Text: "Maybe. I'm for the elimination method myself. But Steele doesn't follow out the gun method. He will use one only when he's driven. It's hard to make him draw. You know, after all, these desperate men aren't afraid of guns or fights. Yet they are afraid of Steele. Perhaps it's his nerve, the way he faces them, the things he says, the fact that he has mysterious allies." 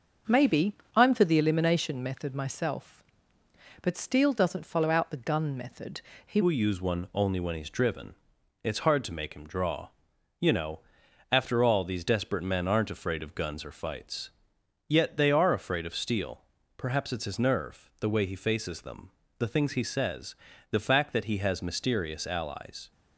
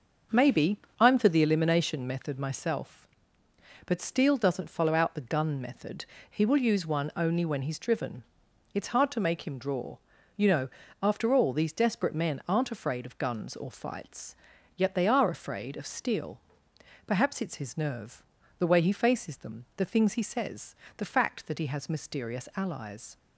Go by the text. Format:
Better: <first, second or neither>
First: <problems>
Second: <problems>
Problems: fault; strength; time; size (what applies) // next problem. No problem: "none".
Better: second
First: starts louder than the rest; until 1.5 s; 6.5 dB // changes voice at "will"; from 6.4 s on; 16.5 s long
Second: starts louder than the rest; until 1.5 s; 6.5 dB